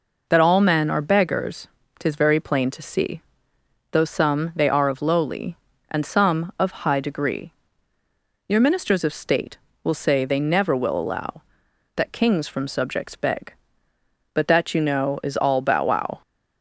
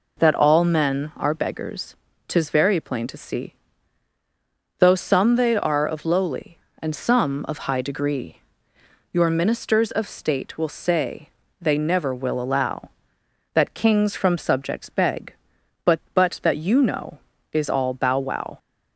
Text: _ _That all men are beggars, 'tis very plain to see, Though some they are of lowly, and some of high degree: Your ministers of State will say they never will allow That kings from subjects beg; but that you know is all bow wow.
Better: first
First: none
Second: pauses between "say" and "they"; slight; at 11.2 s; 0.30 s long // says "but" twice; at 16.1 s

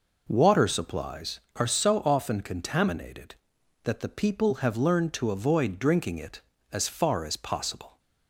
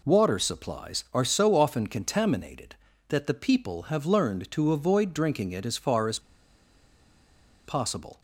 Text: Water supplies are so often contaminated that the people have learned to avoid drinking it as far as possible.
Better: first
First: none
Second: pauses between "as" and "possible"; strong; at 6.1 s; 1.4 s long

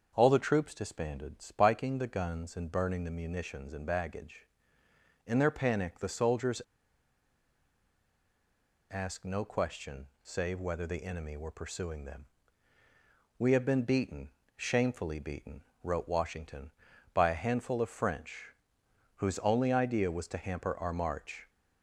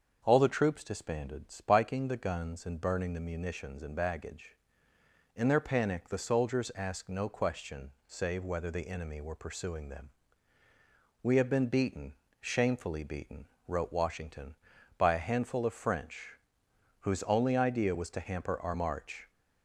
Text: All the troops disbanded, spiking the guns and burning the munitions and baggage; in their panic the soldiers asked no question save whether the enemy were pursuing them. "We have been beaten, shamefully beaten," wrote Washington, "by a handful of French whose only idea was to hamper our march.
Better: second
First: starts louder than the rest; until 1.1 s; 6.5 dB // pauses between "soldiers" and "asked"; strong; at 6.6 s; 2.2 s long // pauses between "question" and "save"; slight; at 10.0 s; 0.16 s long // pauses between "French" and "whose"; noticeable; at 18.5 s; 0.64 s long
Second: starts louder than the rest; until 1.2 s; 6.5 dB // pauses between "question" and "save"; slight; at 7.9 s; 0.16 s long // pauses between "French" and "whose"; noticeable; at 16.3 s; 0.64 s long

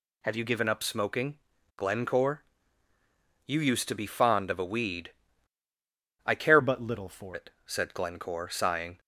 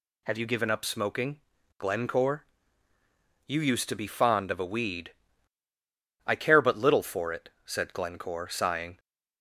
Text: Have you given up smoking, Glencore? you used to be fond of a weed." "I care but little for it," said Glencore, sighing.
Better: second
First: changes voice from "but" to "for"; from 6.6 to 7.3 s; 0.7 s long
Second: none

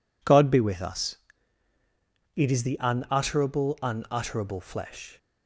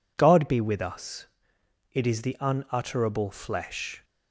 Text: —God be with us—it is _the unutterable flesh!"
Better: second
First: says "unutterable" twice; at 3.8 s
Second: none

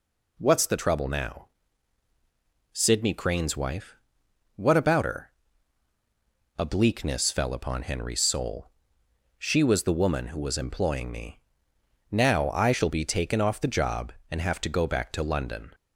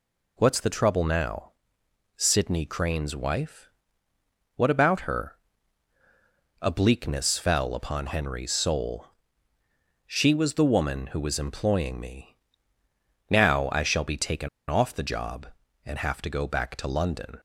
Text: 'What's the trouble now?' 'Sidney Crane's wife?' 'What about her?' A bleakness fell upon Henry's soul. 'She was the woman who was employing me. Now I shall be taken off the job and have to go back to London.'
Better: first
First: none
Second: pauses between "taken" and "off"; slight; at 14.4 s; 0.21 s long

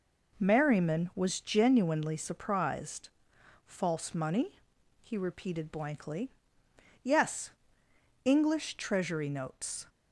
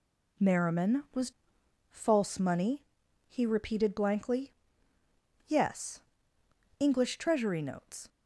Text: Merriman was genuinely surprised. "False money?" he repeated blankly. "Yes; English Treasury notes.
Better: first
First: none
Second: skips "genuinely surprised"; at 1.6 s

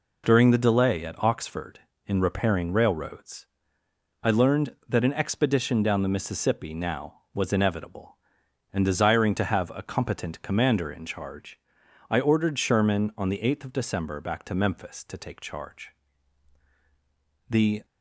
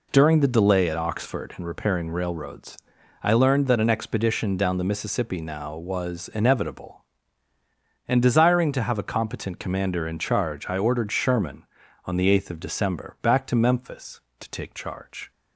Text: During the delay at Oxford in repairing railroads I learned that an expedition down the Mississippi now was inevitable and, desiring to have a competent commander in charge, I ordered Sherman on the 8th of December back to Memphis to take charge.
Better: second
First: pauses between "railroads" and "I"; noticeable; at 3.4 s; 0.78 s long // goes on to say "The"; slight; from 17.5 s on; 0.34 s long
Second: pauses between "railroads" and "I"; at 2.7 s; 0.44 s long

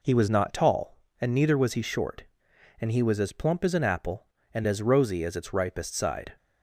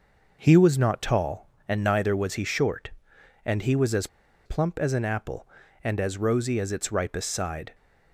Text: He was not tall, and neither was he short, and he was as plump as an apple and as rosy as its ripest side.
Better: first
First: none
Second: pauses between "as" and "plump"; at 4.0 s; 0.38 s long

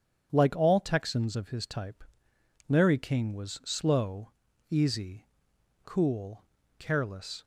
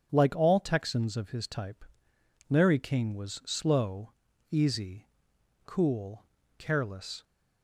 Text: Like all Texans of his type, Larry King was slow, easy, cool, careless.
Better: neither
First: starts louder than the rest; strong; until 1.3 s; 8 dB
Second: starts louder than the rest; strong; until 1.1 s; 8 dB

